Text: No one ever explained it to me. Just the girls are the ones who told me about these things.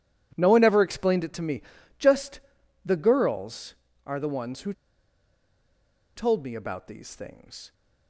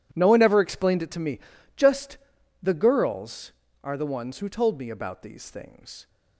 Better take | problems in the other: second | pauses between "Just" and "the"; at 2.3 s; 0.44 s long; also in the second // pauses between "who" and "told"; strong; at 4.7 s; 1.4 s long

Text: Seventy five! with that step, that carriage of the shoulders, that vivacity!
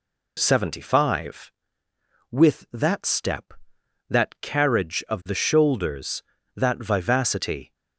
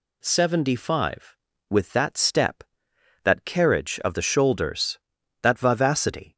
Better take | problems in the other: neither | none

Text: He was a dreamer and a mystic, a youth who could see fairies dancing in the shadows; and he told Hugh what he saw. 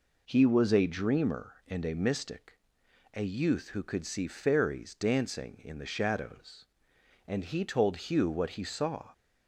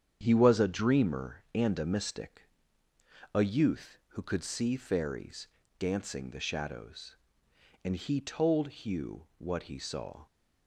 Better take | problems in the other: first | starts louder than the rest; strong; until 1.2 s; 8.5 dB // pauses between "fairies" and "dancing"; slight; at 5.4 s; 0.32 s long // skips "in"; at 6.2 s

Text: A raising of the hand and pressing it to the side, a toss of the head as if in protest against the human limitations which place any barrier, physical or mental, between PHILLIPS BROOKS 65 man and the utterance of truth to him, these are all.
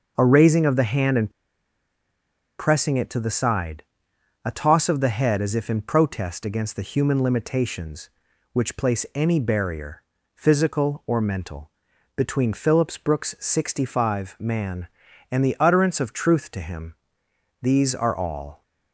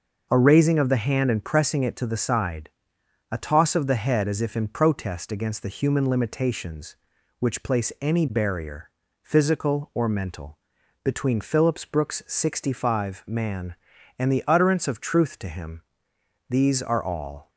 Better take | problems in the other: second | starts louder than the rest; noticeable; until 1.1 s; 6 dB; noticeable in the second // pauses between "and" and "pressing"; strong; at 1.2 s; 1.2 s long

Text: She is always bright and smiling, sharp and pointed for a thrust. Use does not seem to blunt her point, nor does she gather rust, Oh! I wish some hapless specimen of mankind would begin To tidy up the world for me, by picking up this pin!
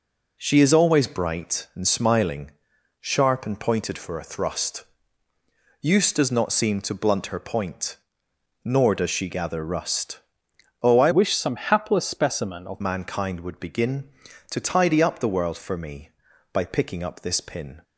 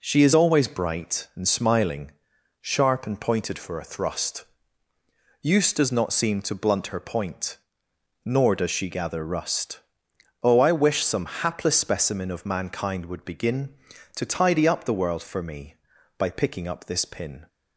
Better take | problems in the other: second | changes voice from "wish" to "of"; from 11.1 to 12.8 s; 1.7 s long

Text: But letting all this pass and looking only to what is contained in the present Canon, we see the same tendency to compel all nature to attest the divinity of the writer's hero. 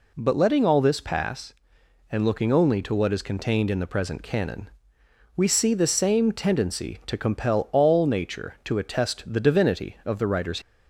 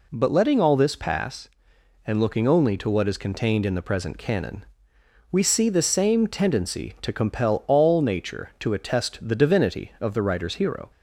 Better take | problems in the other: second | stops before "hero"; at 10.6 s

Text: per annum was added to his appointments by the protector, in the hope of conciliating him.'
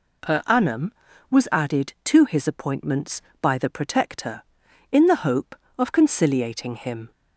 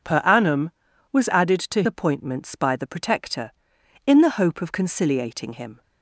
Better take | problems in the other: first | skips "his"; at 1.8 s

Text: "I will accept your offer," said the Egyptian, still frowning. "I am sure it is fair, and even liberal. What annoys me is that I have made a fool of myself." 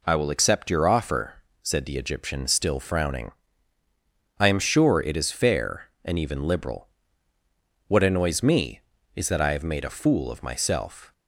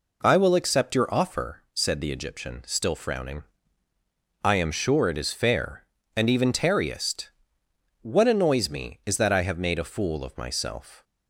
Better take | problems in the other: first | says "tarriest" for "liberal"; at 6.5 s

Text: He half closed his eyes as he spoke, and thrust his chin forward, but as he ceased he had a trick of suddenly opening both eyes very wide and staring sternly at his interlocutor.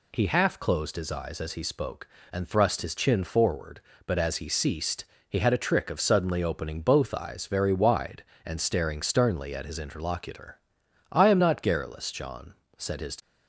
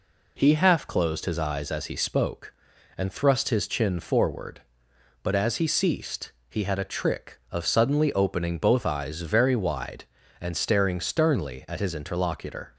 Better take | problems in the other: second | pauses between "ceased" and "he"; slight; at 5.0 s; 0.24 s long; slight in the second // goes on to say "I am not garrulous John said his"; strong; from 11.1 s on; 2.0 s long

